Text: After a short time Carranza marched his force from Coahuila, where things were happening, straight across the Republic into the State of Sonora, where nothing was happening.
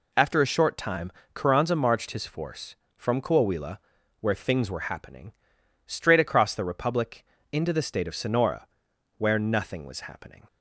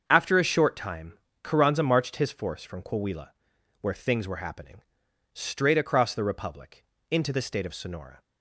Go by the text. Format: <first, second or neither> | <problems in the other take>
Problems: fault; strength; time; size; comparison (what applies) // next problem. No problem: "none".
first | starts louder than the rest; until 1.0 s; 7 dB // pauses between "time" and "Carranza"; slight; at 1.1 s; 0.28 s long; slight in the first // pauses between "Republic" and "into"; slight; at 6.8 s; 0.26 s long; slight in the first // stops before "where nothing was happening"; at 8.2 s